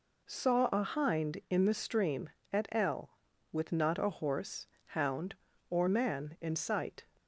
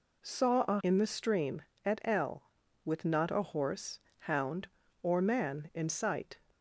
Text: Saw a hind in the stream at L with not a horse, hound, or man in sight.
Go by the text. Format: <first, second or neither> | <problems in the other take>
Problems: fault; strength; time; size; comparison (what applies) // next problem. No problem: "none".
first | skips "hind"; at 0.8 s